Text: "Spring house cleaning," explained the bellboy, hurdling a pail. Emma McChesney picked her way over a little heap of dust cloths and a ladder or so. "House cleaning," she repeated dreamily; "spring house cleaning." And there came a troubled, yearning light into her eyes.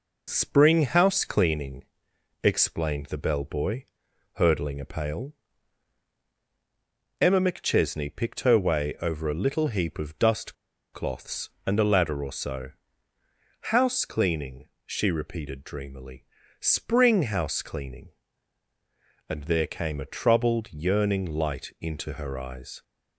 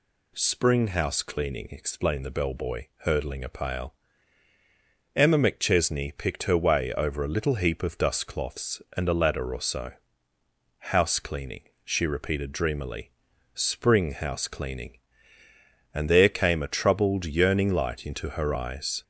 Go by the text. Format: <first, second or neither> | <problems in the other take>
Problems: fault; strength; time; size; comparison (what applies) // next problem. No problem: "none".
second | pauses between "dust" and "cloths"; at 10.5 s; 0.38 s long